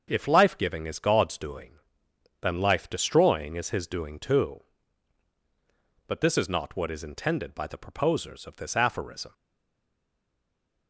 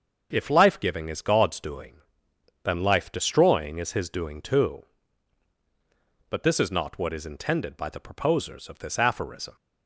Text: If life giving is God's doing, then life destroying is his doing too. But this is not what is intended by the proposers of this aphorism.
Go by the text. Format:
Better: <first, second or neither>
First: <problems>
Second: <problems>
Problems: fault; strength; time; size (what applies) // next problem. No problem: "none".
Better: second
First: starts louder than the rest; until 1.0 s; 6.5 dB // stays silent after the last word; noticeable; from 9.3 s on; 1.5 s long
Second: starts louder than the rest; until 1.3 s; 6.5 dB